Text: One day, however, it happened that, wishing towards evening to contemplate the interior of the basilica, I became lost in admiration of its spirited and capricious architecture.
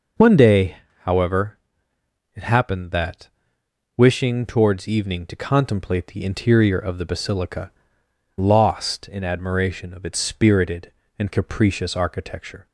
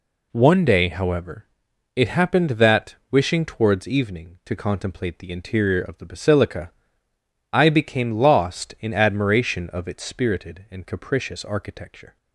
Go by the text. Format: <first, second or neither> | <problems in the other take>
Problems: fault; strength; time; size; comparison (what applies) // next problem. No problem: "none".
second | skips "I became"; at 8.0 s